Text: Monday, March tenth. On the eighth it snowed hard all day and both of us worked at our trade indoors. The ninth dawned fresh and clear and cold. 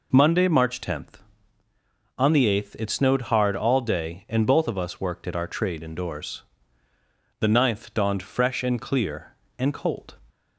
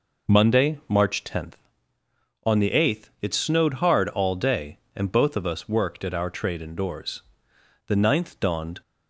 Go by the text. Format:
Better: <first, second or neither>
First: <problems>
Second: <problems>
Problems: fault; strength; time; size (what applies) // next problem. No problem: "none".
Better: first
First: none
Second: stops before "fresh and clear and cold"; at 8.8 s